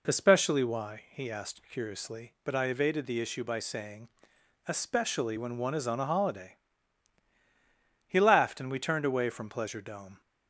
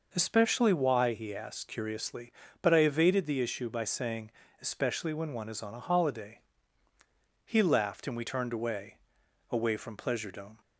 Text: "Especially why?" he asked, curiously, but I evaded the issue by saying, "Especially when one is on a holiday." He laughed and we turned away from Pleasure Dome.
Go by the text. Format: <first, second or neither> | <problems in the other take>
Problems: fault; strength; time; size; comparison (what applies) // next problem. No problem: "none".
first | says "away" twice; at 9.5 s